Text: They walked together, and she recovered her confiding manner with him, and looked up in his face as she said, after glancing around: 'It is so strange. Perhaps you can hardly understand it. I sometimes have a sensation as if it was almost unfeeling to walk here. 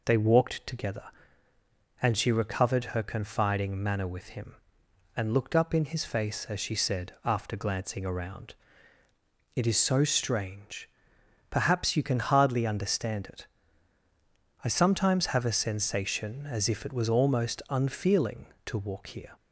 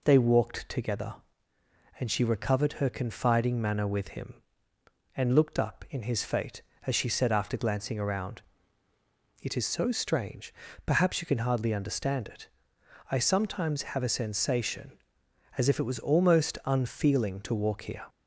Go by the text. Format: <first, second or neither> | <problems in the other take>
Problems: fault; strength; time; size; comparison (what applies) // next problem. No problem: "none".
first | says "fate" for "face"; at 6.2 s